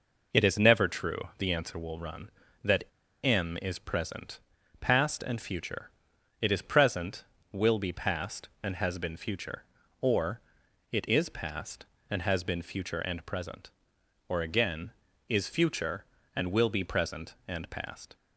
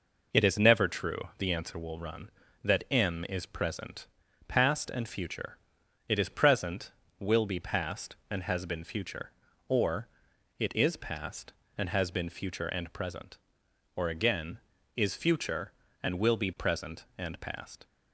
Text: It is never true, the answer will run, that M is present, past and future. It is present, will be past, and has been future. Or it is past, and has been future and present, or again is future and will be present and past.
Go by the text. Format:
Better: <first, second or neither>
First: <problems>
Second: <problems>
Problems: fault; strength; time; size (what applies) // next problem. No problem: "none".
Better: second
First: pauses between "that" and "M"; at 2.8 s; 0.38 s long // pauses between "Or" and "it"; noticeable; at 10.3 s; 0.52 s long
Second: pauses between "Or" and "it"; noticeable; at 10.0 s; 0.52 s long